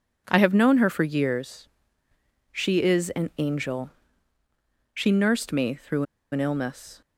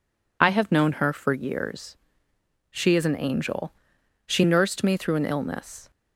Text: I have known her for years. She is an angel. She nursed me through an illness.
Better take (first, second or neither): second